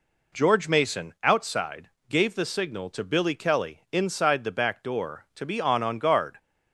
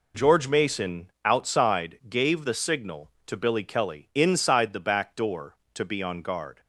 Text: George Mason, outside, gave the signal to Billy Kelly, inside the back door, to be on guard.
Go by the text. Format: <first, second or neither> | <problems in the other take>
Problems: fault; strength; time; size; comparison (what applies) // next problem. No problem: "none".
second | says "on" twice; at 5.8 s